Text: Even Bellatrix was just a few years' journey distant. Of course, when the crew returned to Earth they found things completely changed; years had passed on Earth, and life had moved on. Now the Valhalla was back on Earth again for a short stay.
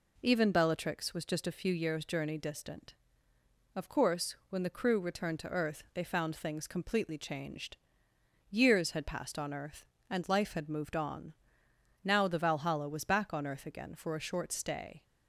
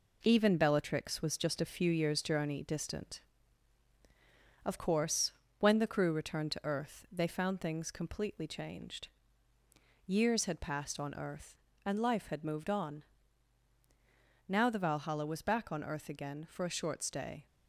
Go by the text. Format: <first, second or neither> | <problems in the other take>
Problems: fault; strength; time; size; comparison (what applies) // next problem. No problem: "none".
first | gets quieter; noticeable; throughout; 5 dB